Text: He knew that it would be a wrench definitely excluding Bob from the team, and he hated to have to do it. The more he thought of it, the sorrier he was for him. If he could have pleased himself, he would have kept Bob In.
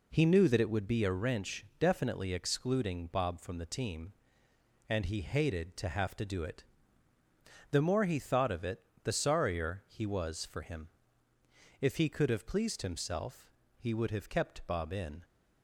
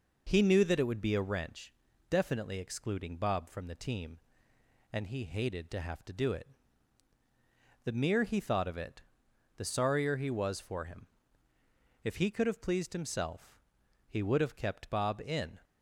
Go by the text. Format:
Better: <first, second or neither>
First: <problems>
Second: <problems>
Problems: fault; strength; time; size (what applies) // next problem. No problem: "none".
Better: first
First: none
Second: pauses between "wrench" and "definitely"; at 1.7 s; 0.38 s long // says "mere" for "more"; at 7.9 s